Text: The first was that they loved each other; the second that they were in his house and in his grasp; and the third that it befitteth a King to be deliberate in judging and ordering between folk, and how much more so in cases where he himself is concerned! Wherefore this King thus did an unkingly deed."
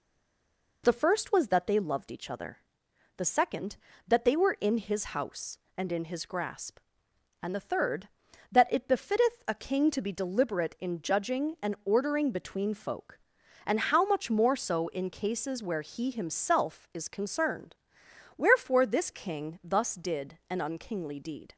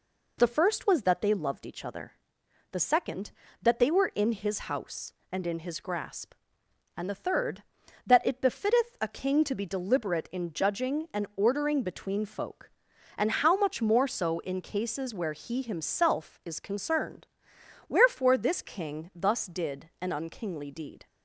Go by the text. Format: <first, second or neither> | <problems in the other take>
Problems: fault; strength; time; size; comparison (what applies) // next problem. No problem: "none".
second | stays silent before the first word; slight; until 0.8 s; 0.8 s long